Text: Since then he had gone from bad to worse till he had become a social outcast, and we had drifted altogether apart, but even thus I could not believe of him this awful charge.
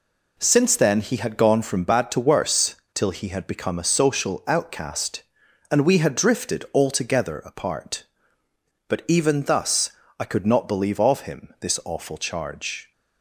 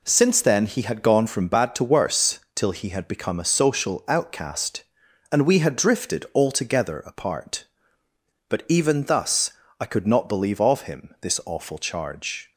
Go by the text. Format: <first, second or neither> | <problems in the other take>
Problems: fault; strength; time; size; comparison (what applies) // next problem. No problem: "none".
neither | pauses between "worse" and "till"; slight; the same in both // pauses between "thus" and "I"; slight; the same in both